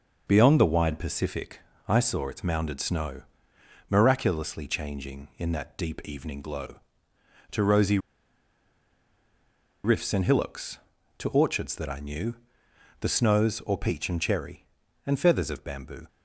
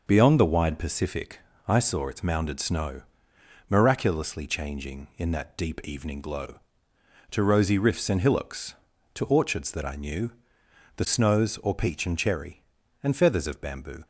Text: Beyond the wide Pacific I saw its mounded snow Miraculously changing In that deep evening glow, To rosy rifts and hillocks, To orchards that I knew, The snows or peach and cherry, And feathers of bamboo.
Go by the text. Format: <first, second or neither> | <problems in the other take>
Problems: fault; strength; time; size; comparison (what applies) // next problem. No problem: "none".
second | pauses between "Pacific" and "I"; slight; at 1.5 s; 0.28 s long; slight in the second // pauses between "snow" and "Miraculously"; noticeable; at 3.2 s; 0.66 s long; noticeable in the second // pauses between "rosy" and "rifts"; strong; at 7.9 s; 1.8 s long